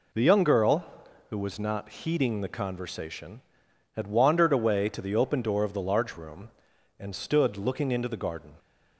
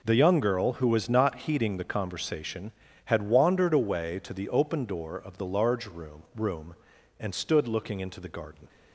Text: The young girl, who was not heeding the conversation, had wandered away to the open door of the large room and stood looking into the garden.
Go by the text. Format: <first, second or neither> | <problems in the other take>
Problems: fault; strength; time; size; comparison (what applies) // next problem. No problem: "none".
first | says "room" twice; at 6.3 s